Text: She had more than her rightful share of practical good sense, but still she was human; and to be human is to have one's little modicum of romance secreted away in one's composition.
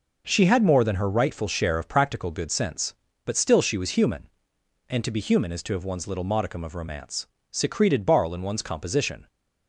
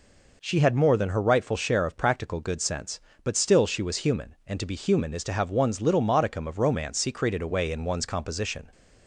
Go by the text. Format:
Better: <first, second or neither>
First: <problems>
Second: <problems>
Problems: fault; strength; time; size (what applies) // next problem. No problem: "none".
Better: second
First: pauses between "romance" and "secreted"; slight; at 7.2 s; 0.24 s long // says "barl" for "away"; at 8.0 s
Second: none